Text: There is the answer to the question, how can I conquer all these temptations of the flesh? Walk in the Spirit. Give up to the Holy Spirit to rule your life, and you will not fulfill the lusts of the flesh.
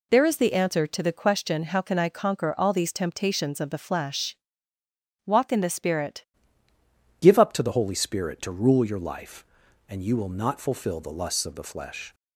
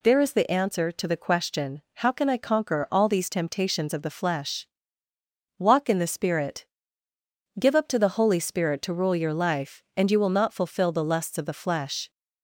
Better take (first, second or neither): second